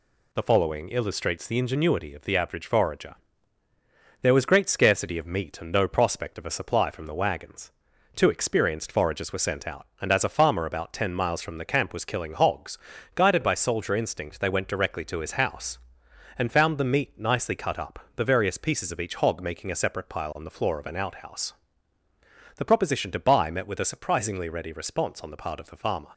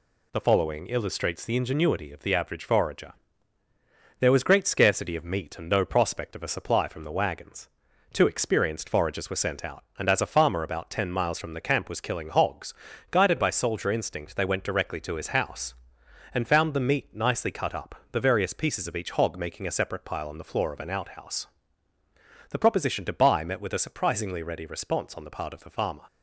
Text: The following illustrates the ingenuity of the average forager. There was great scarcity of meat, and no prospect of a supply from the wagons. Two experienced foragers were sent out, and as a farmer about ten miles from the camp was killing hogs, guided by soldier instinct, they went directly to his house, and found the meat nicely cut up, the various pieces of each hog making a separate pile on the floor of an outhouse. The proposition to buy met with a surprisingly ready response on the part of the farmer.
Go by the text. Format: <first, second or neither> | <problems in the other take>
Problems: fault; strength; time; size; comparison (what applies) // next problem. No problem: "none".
neither | none